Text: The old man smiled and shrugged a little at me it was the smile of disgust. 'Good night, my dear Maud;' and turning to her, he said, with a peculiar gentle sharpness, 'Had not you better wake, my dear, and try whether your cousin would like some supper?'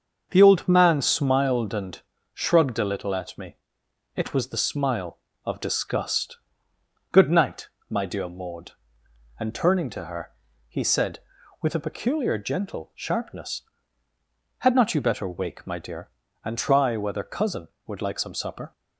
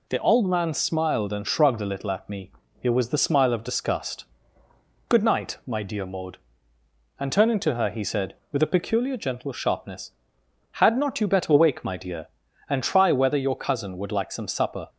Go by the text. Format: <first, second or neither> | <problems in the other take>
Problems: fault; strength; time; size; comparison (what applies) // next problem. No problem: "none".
second | starts louder than the rest; until 1.3 s; 6.5 dB // pauses between "and" and "shrugged"; slight; at 1.9 s; 0.34 s long // pauses between "me" and "it"; noticeable; at 3.5 s; 0.58 s long; slight in the second // skips "your"; at 17.2 s